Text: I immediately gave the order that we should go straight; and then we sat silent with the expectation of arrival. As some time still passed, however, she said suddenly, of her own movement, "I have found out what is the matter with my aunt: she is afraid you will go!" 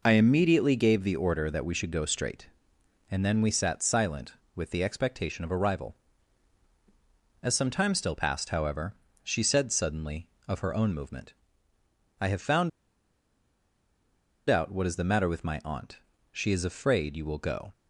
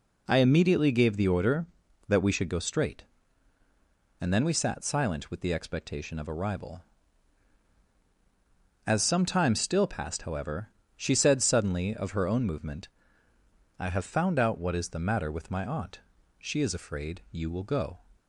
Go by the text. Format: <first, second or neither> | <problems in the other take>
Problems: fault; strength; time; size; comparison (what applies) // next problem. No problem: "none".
second | pauses between "found" and "out"; strong; at 12.6 s; 1.7 s long